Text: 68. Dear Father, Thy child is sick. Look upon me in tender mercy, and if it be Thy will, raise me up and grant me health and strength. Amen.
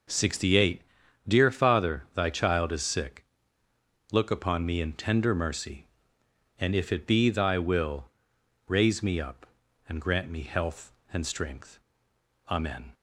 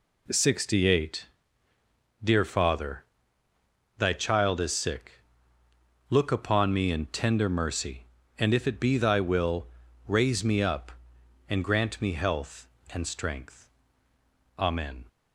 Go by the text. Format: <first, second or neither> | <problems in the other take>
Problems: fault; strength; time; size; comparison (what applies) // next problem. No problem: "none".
neither | none